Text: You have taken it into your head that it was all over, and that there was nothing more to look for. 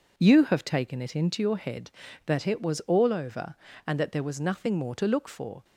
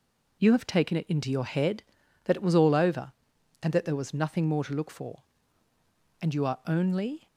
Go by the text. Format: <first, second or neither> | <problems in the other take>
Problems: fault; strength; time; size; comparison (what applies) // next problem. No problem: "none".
first | goes on to say "And you are only"; noticeable; from 6.2 s on; 1.0 s long